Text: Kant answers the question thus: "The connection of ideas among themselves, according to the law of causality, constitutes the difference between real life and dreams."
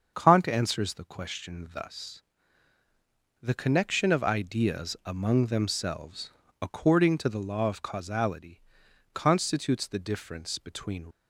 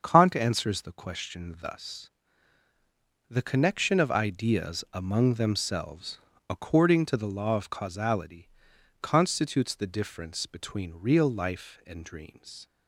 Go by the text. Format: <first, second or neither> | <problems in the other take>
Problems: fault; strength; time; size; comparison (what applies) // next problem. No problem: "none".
second | starts louder than the rest; until 1.1 s; 7 dB; also in the second // stops before "real life and dreams"; at 11.1 s